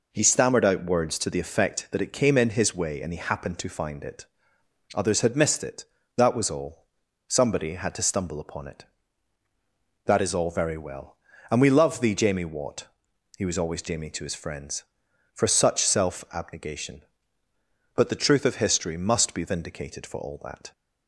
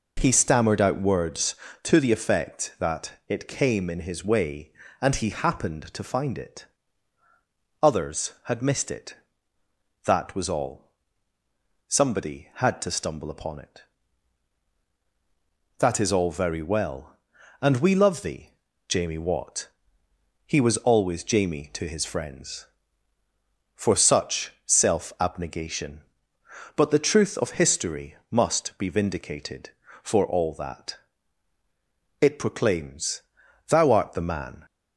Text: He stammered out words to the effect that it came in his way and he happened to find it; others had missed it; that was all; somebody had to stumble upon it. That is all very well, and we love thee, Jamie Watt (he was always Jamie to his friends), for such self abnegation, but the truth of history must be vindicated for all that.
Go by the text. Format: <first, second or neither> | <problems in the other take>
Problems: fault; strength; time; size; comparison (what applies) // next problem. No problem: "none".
first | pauses between "that" and "it"; slight; at 3.1 s; 0.16 s long // pauses between "history" and "must"; slight; at 28.1 s; 0.16 s long // goes on to say "It proclaims Thou art the man"; strong; from 32.2 s on; 2.4 s long